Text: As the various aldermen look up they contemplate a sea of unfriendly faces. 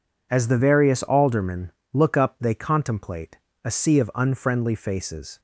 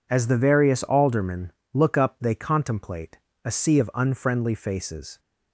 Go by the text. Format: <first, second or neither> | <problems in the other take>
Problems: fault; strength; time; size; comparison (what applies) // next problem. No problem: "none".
neither | pauses between "aldermen" and "look"; slight; the same in both // pauses between "contemplate" and "a"; slight; the same in both